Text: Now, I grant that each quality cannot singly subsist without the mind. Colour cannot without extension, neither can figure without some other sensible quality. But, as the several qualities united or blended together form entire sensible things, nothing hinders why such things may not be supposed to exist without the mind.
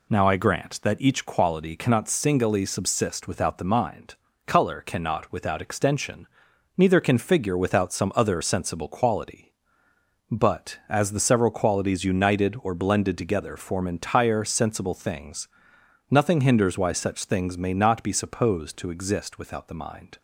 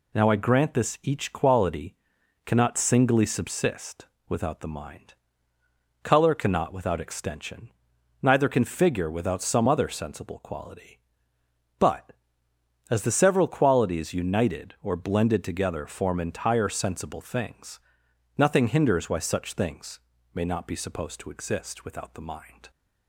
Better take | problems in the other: first | says "this" for "that"; at 0.7 s // pauses between "quality" and "cannot"; noticeable; at 1.9 s; 0.48 s long // pauses between "subsist" and "without"; slight; at 4.0 s; 0.22 s long // pauses between "things" and "may"; slight; at 19.9 s; 0.36 s long

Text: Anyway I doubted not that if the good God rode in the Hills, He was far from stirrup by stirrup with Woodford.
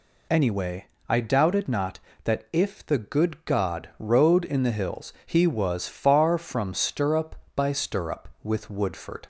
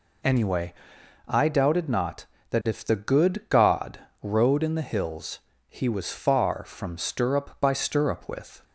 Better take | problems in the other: first | pauses between "Anyway" and "I"; noticeable; at 0.7 s; 0.56 s long; slight in the first // pauses between "God" and "rode"; slight; at 3.9 s; 0.22 s long // stops before "Woodford"; at 8.6 s

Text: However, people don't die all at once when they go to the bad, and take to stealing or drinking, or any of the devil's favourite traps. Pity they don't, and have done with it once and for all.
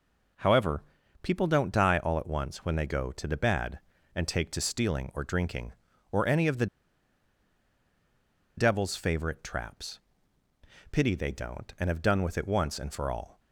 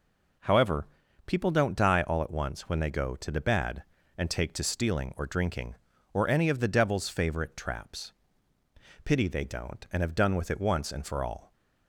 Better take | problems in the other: second | pauses between "the" and "devil's"; strong; at 6.6 s; 1.9 s long

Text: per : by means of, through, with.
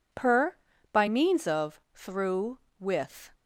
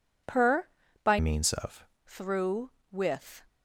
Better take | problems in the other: first | changes voice from "means" to "of"; from 1.1 to 1.8 s; 0.7 s long

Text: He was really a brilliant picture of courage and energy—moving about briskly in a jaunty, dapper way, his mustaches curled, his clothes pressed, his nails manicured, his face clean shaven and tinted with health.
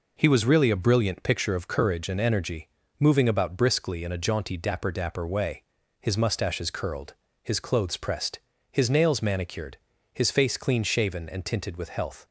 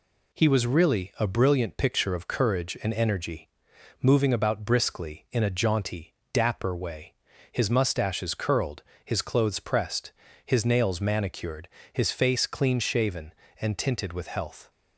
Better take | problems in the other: second | says "dapper" twice; at 4.8 s

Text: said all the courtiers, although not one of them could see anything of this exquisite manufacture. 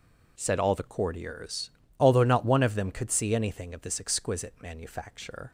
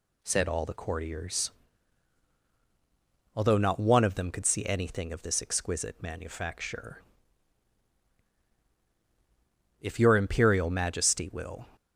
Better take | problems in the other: first | goes on to say "If your Imperial Majesty will"; strong; from 9.7 s on; 1.8 s long

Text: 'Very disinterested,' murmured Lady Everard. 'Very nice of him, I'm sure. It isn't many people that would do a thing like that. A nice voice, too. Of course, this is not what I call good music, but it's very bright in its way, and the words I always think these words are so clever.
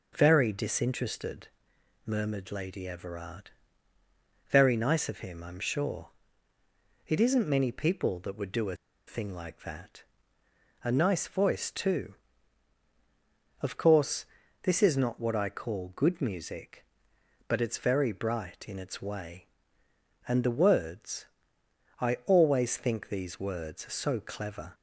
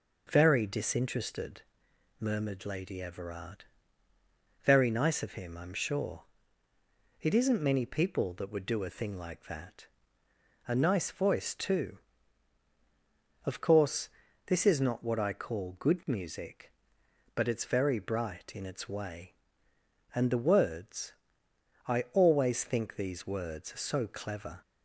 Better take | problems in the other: second | pauses between "a" and "thing"; slight; at 8.7 s; 0.31 s long // pauses between "words" and "I"; noticeable; at 21.2 s; 0.78 s long; noticeable in the second

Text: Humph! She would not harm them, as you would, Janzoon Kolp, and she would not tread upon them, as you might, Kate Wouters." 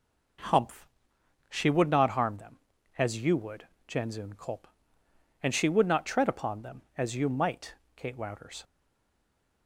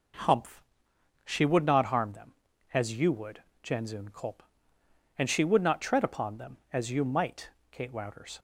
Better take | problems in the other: second | stays silent after the last word; from 8.6 s on; 1.0 s long

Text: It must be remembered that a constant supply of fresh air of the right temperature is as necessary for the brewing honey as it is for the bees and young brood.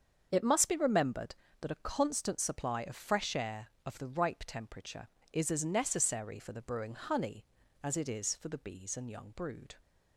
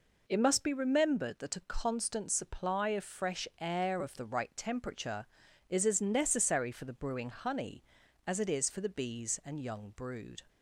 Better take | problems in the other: second | starts louder than the rest; until 1.3 s; 7 dB // says "ripe" for "right"; at 4.0 s

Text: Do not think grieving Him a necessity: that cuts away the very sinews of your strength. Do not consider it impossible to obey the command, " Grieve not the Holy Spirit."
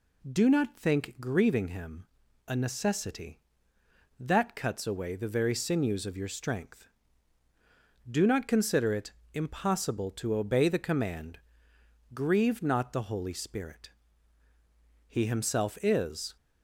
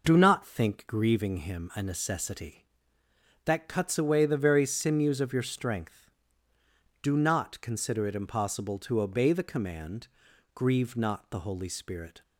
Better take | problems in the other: second | pauses between "Him" and "a"; at 2.0 s; 0.40 s long // pauses between "it" and "impossible"; slight; at 9.0 s; 0.24 s long // goes on to say "He Himself is"; noticeable; from 15.0 s on; 1.2 s long

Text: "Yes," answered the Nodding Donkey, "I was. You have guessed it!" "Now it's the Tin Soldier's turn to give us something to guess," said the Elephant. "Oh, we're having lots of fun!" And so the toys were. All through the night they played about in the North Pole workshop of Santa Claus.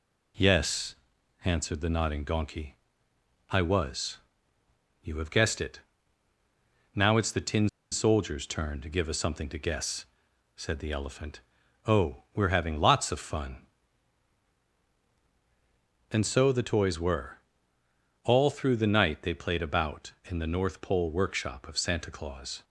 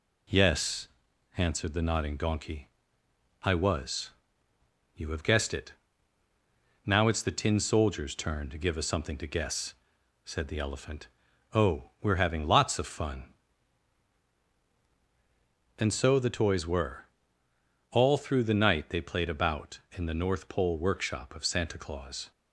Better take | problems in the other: second | pauses between "Tin" and "Soldier's"; slight; at 7.6 s; 0.22 s long

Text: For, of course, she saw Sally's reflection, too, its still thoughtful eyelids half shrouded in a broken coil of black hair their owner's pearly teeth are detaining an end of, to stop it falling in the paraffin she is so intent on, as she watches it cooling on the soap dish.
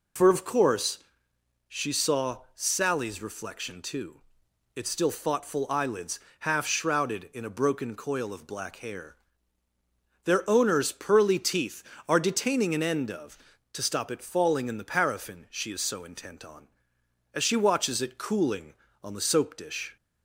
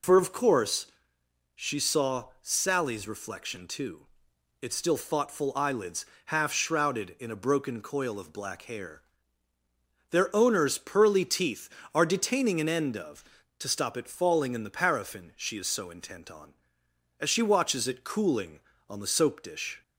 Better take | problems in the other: neither | pauses between "saw" and "Sally's"; slight; the same in both // pauses between "eyelids" and "half"; slight; the same in both // pauses between "hair" and "their"; the same in both

